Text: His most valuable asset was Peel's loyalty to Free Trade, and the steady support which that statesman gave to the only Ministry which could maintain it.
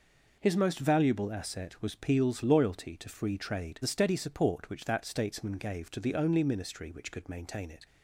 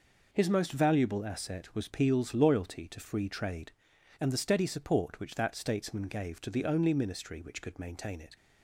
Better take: second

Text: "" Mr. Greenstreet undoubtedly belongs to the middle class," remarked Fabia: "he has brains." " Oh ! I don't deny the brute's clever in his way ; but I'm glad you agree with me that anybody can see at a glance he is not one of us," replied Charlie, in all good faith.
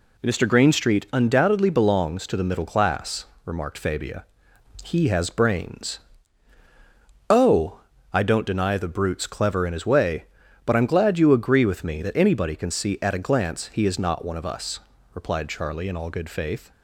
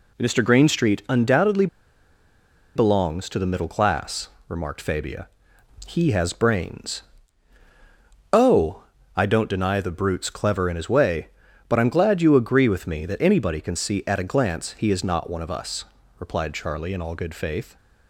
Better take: first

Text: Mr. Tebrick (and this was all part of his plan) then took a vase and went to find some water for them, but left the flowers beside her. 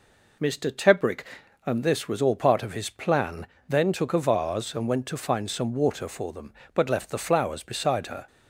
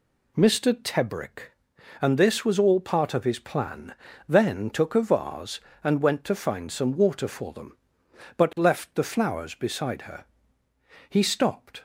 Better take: first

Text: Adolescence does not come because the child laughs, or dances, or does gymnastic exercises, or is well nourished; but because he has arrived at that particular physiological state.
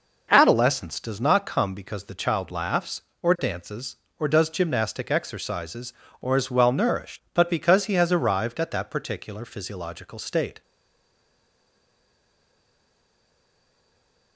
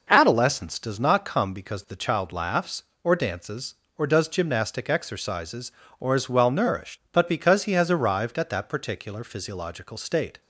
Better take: second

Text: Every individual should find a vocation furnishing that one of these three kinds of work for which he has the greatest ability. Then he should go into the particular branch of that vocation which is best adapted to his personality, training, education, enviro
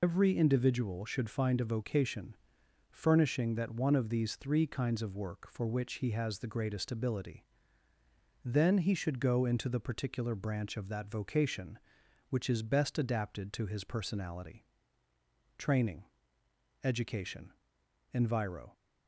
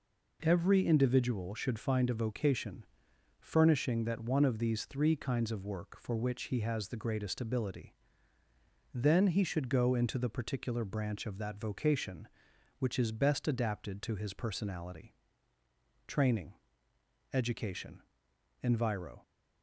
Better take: second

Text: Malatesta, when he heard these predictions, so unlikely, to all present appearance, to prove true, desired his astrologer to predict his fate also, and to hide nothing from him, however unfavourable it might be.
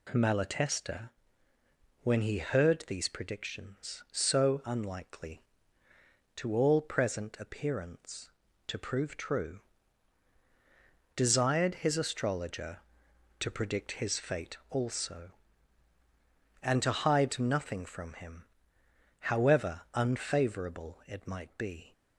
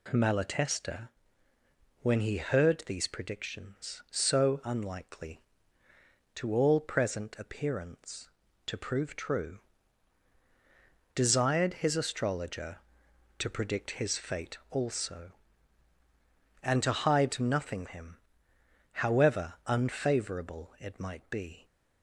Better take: first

